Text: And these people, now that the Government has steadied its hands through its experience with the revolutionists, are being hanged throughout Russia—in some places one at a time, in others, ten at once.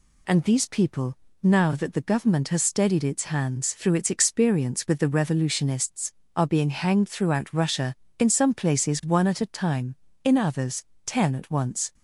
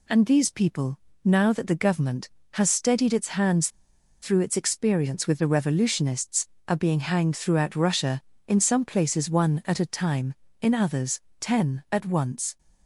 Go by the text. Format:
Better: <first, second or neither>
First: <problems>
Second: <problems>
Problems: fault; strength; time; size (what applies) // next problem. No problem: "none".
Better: first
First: none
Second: pauses between "hands" and "through"; noticeable; at 3.6 s; 0.53 s long